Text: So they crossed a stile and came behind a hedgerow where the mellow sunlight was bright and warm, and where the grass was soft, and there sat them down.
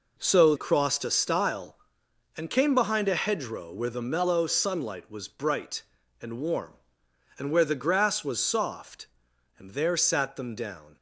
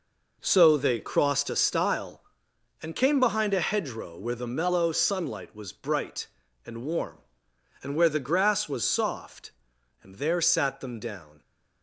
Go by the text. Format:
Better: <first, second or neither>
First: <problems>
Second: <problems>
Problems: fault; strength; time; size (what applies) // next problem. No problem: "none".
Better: second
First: skips "they"; at 0.5 s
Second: none